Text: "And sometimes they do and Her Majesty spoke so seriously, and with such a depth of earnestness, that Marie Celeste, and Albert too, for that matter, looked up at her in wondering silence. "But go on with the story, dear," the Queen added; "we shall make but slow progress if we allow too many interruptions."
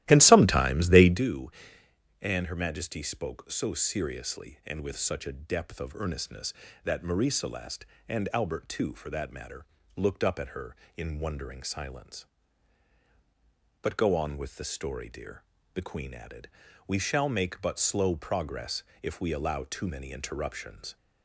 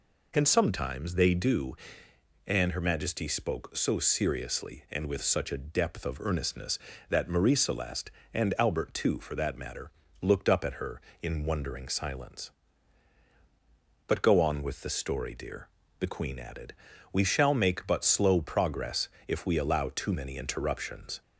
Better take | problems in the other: second | starts louder than the rest; strong; until 1.2 s; 15 dB // pauses between "progress" and "if"; slight; at 18.8 s; 0.20 s long; slight in the second

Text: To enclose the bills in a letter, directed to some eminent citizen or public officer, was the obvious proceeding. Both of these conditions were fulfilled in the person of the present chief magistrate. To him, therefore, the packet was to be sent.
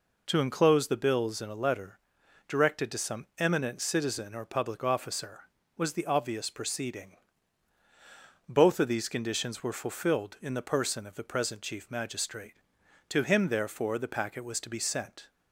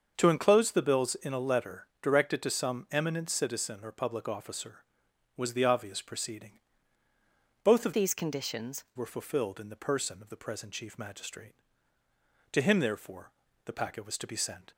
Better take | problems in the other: first | starts louder than the rest; until 1.1 s; 6.5 dB // changes voice from "these" to "conditions"; from 7.9 to 8.8 s; 0.9 s long

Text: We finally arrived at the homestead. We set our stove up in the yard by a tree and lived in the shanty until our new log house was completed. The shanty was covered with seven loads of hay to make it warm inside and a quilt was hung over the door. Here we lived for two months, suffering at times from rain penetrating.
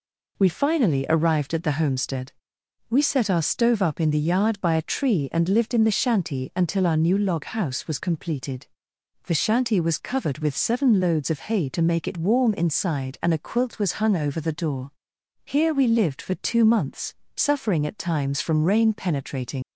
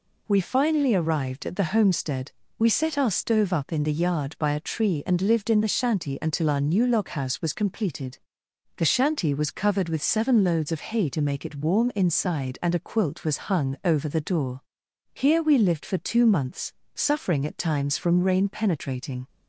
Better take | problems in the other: second | leaves "penetrating" unfinished; at 19.6 s; 85 ms

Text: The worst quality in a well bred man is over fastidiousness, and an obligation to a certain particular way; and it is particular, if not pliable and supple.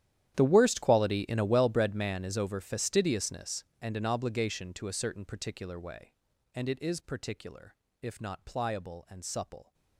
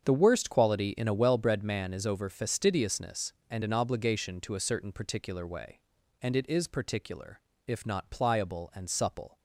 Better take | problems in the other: second | gets quieter; strong; throughout; 20 dB // starts louder than the rest; strong; until 1.3 s; 11 dB; strong in the second

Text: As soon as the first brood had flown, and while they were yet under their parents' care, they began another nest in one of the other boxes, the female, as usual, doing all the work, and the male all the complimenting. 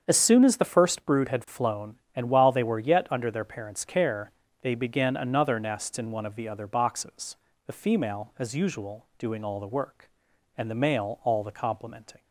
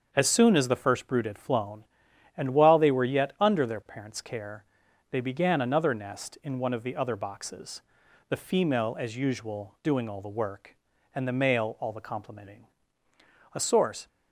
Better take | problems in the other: first | starts louder than the rest; until 1.1 s; 7 dB; strong in the first // goes on to say "A source"; from 13.5 s on; 0.54 s long

